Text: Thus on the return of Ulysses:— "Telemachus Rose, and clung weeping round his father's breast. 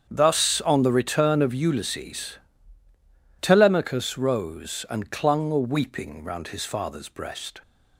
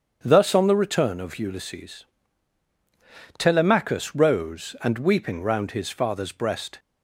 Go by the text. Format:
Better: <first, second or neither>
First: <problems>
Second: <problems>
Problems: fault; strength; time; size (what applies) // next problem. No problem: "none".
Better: first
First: starts louder than the rest; strong; until 1.1 s; 8 dB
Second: starts louder than the rest; strong; until 1.2 s; 7.5 dB // skips "clung"; at 4.9 s